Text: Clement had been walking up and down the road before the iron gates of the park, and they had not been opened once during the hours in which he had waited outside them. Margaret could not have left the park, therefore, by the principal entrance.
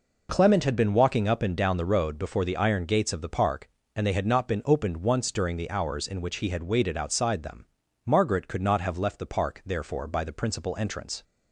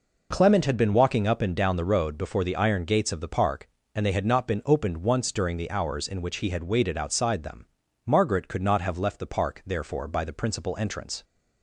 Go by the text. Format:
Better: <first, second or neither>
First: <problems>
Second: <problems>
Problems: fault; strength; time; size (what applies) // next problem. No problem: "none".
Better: neither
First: none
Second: none